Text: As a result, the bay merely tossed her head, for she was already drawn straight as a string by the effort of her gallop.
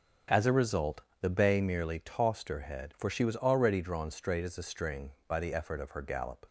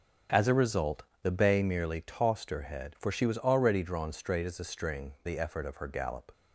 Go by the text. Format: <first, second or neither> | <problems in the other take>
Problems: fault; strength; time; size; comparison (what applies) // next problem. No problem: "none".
first | starts louder than the rest; until 1.5 s; 7 dB; also in the first // skips "by"; at 5.1 s